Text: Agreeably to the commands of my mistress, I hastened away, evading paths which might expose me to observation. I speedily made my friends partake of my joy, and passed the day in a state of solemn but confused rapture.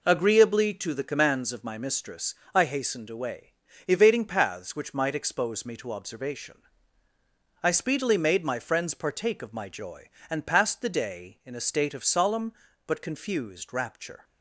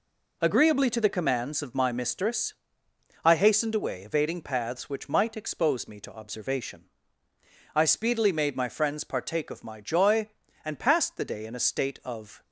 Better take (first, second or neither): first